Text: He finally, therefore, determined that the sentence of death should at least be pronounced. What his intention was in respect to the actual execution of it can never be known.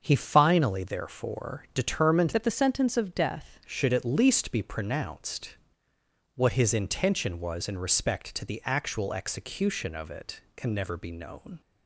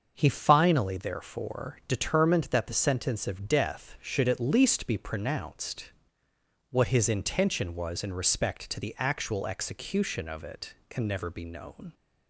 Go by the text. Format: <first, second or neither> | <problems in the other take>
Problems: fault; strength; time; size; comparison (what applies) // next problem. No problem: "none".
second | starts louder than the rest; until 1.0 s; 6.5 dB; also in the second // changes voice from "that" to "death"; from 2.3 to 3.5 s; 1.2 s long